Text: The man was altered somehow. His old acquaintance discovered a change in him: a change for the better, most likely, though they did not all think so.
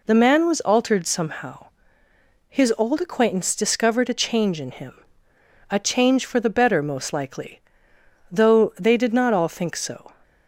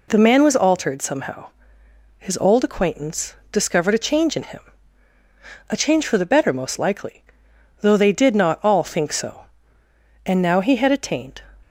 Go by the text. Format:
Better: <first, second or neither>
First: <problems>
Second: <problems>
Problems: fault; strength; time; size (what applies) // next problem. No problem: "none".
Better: first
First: none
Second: pauses between "acquaintance" and "discovered"; slight; at 3.3 s; 0.16 s long // goes on to say "And now he had attained"; noticeable; from 10.2 s on; 1.1 s long